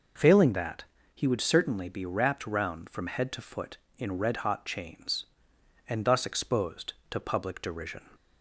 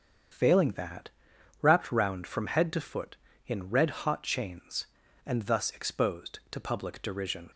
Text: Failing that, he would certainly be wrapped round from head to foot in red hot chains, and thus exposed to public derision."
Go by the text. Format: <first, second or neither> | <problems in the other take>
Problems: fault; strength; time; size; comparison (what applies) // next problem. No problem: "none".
first | starts louder than the rest; strong; until 1.8 s; 7.5 dB // skips "he would certainly be"; at 1.3 s